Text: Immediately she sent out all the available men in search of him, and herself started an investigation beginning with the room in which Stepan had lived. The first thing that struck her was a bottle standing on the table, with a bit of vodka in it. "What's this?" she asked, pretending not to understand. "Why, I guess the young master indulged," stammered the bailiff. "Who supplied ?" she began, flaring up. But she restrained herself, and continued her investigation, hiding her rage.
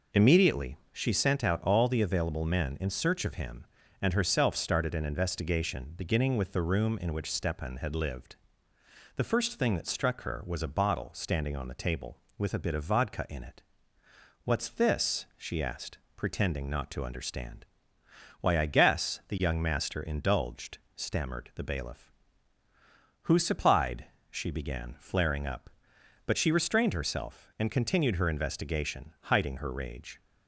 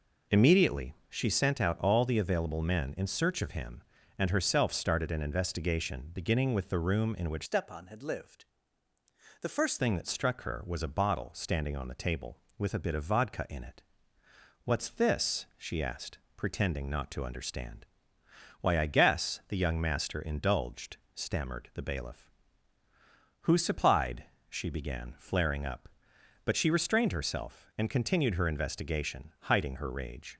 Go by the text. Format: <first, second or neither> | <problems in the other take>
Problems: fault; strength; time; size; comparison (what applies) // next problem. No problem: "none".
first | pauses between "Immediately" and "she"; slight; at 0.9 s; 0.16 s long; slight in the first // changes voice from "Stepan" to "first"; from 7.4 to 9.7 s; 2.3 s long